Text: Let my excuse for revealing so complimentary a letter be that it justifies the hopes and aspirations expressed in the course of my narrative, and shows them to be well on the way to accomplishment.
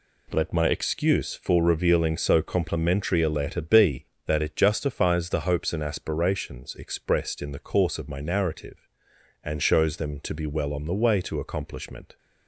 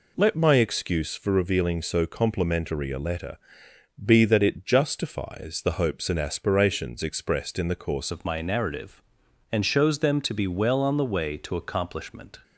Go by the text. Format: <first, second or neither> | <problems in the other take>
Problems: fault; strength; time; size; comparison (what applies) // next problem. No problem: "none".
first | pauses between "letter" and "be"; noticeable; at 3.3 s; 0.66 s long // changes voice at "of"; from 8.1 s on; 4.3 s long